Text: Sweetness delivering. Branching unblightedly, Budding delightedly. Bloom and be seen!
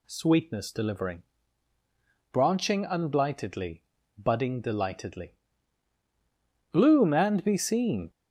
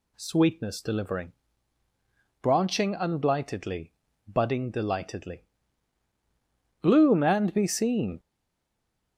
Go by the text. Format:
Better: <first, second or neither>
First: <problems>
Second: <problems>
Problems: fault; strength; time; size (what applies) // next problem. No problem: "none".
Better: first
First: none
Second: stays silent after the last word; slight; from 8.1 s on; 1.0 s long